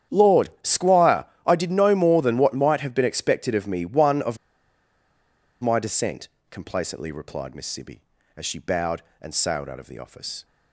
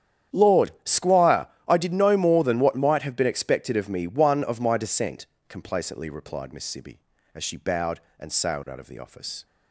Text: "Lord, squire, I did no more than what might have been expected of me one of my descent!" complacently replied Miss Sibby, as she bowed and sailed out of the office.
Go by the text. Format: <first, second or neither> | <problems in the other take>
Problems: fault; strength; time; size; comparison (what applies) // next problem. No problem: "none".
second | starts louder than the rest; strong; until 1.2 s; 9.5 dB; strong in the second // pauses between "of" and "my"; strong; at 4.3 s; 1.2 s long